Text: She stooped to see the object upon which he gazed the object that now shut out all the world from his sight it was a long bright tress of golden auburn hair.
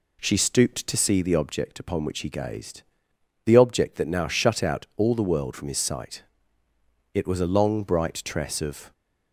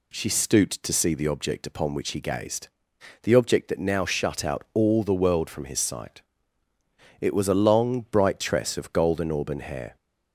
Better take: second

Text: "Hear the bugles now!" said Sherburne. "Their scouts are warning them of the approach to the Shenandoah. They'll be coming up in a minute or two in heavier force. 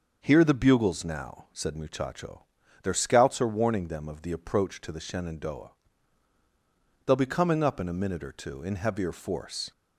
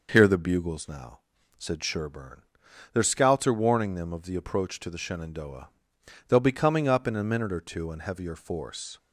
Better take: second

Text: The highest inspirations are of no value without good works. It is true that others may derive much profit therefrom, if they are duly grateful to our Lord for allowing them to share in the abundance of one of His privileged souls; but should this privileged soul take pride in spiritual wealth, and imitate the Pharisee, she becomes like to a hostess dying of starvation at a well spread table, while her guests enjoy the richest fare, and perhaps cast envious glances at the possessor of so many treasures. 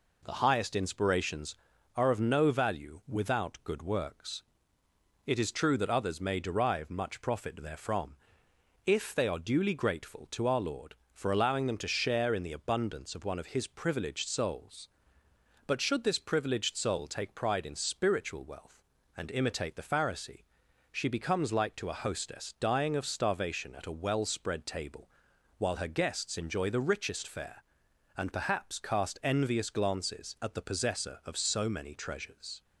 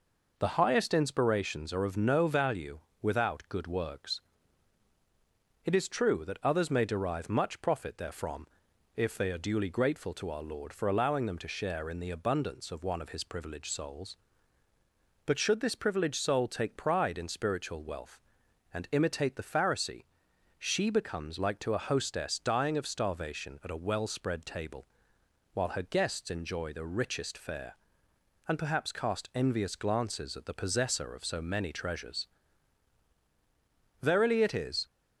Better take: first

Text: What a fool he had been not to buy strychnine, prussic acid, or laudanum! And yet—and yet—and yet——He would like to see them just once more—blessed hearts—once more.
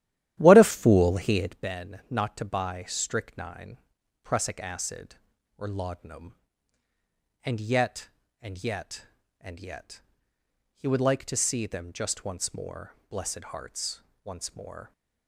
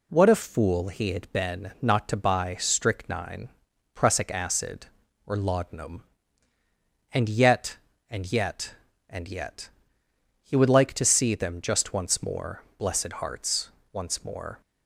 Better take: second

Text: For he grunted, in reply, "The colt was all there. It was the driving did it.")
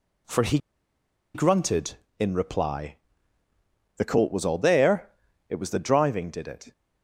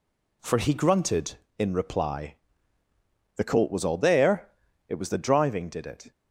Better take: second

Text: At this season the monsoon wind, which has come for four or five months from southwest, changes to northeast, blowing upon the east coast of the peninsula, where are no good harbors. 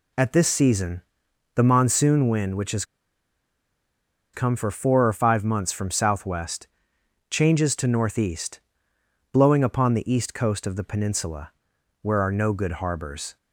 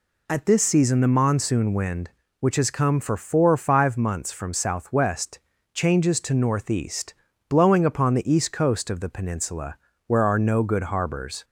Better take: second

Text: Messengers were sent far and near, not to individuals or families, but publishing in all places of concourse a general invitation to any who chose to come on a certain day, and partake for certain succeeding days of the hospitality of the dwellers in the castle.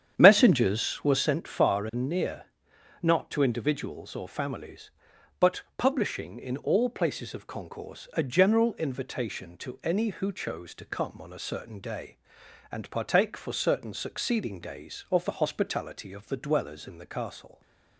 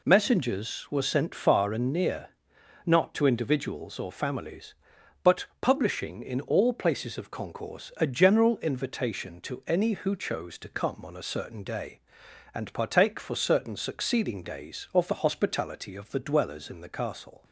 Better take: second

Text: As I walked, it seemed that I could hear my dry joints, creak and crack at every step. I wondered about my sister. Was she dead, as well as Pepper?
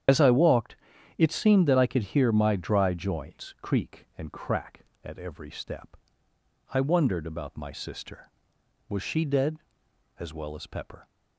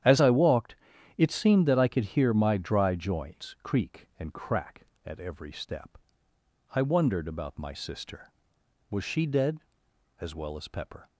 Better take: second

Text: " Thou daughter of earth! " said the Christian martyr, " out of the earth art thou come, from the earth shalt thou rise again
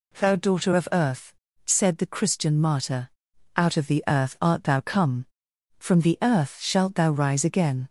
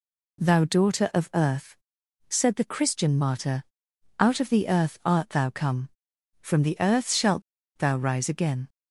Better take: first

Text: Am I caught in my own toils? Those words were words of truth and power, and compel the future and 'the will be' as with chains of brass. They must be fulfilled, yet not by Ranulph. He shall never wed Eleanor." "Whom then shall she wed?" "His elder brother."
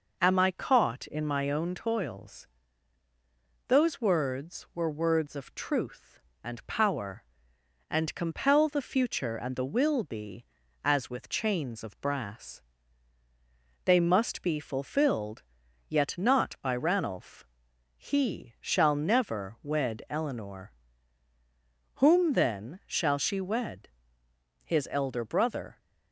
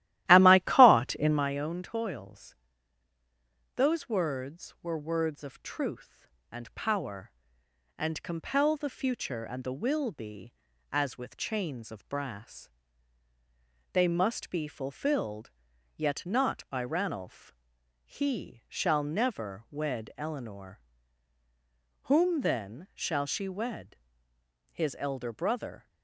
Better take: first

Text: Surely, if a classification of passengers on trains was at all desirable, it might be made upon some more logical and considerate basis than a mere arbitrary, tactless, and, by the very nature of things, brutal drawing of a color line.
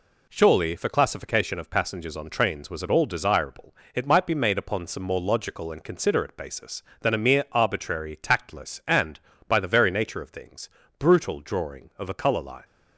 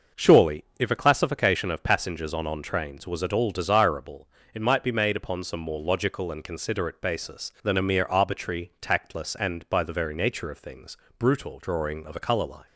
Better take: first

